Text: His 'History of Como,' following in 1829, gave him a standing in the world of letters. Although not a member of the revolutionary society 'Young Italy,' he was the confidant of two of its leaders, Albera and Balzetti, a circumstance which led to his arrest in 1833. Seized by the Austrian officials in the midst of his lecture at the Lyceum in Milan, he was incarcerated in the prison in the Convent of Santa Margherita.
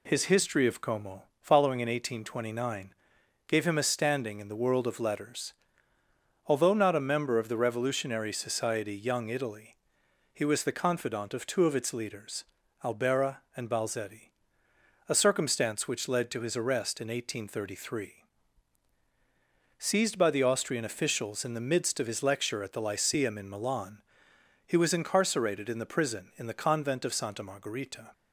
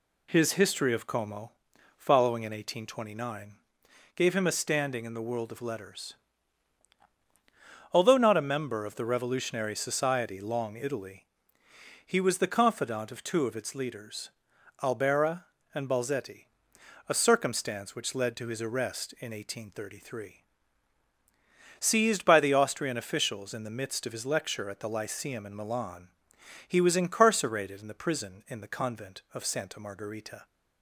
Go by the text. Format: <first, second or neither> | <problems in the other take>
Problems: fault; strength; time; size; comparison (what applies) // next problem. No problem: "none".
first | says "Long" for "Young"; at 10.3 s